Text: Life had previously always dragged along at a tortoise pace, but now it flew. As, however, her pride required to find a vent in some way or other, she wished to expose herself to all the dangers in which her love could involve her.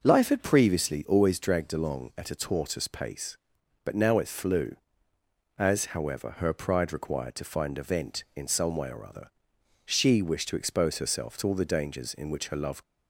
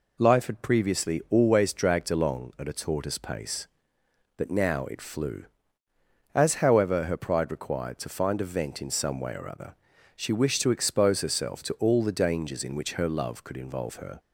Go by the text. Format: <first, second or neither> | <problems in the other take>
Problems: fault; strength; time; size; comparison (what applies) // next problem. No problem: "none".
second | stops before "could involve her"; at 12.8 s